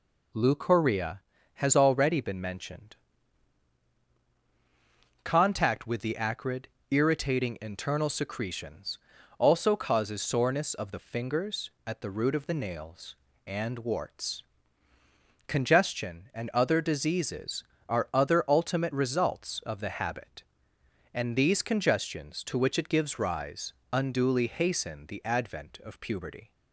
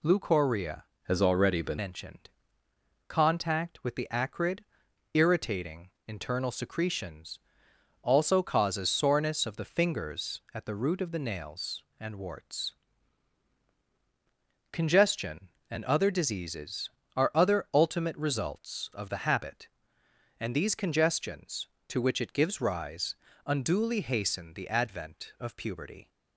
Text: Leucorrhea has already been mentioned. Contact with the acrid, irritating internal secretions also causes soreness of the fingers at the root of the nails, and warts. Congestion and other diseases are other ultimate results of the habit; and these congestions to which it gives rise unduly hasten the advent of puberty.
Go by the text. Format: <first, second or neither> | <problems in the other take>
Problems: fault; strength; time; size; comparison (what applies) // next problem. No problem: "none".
first | changes voice from "has" to "been"; from 1.0 to 1.7 s; 0.7 s long // pauses between "irritating" and "internal"; slight; at 5.9 s; 0.16 s long // pauses between "secretions" and "also"; noticeable; at 7.3 s; 0.62 s long; also in the first // pauses between "rise" and "unduly"; slight; at 23.1 s; 0.30 s long; slight in the first